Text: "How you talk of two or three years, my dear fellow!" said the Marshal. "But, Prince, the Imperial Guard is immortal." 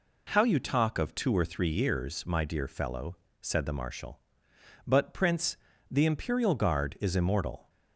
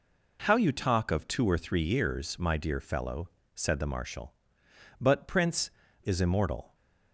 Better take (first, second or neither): first